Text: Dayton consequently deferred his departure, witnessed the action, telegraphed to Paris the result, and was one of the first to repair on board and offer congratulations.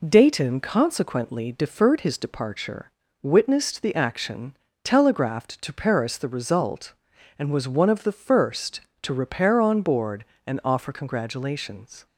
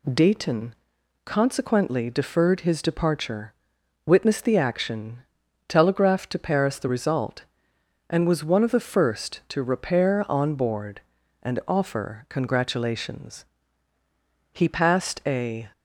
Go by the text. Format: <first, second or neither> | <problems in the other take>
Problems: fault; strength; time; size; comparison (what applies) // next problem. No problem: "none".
first | pauses between "Dayton" and "consequently"; noticeable; at 0.7 s; 0.50 s long // goes on to say "He passed a"; noticeable; from 14.5 s on; 1.2 s long